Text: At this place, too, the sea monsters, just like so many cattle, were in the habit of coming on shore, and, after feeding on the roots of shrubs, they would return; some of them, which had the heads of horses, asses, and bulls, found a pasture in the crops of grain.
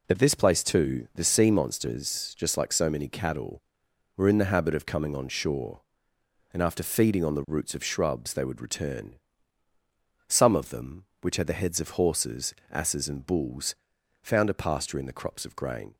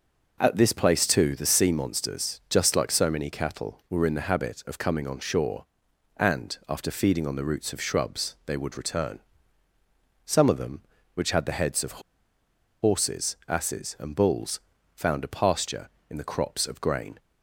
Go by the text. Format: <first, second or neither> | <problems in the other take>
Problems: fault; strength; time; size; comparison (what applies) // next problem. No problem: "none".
first | pauses between "of" and "horses"; noticeable; at 12.0 s; 0.80 s long